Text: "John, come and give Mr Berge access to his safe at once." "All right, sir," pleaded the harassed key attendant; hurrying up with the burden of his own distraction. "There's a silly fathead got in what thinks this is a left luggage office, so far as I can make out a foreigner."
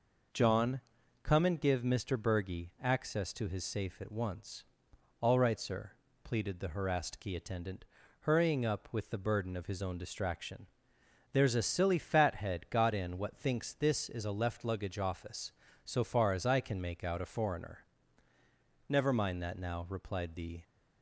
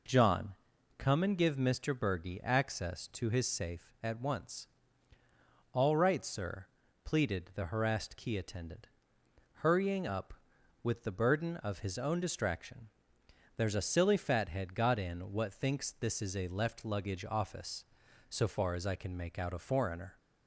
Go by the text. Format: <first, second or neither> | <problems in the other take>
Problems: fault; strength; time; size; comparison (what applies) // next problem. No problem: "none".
second | goes on to say "Never mind that now replied the"; strong; from 18.8 s on; 1.7 s long